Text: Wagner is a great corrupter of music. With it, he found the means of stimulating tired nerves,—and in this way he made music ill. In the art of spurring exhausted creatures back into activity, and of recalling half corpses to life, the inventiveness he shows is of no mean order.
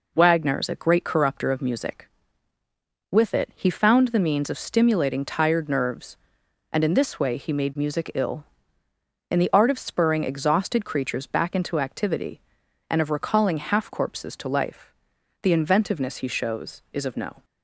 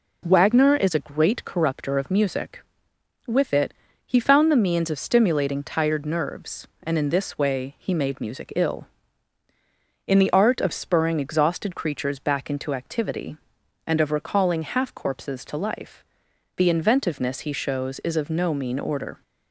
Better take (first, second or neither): second